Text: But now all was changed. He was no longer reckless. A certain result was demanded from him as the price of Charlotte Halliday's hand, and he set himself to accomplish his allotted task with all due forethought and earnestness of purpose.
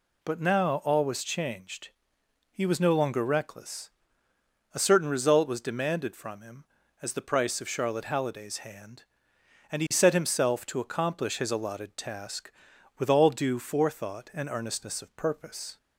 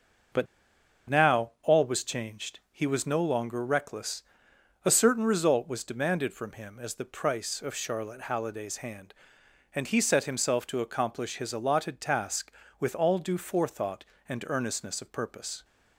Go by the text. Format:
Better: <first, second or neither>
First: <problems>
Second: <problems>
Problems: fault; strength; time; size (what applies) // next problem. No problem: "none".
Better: first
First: none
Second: starts louder than the rest; until 2.0 s; 6 dB // pauses between "But" and "now"; noticeable; at 0.4 s; 0.64 s long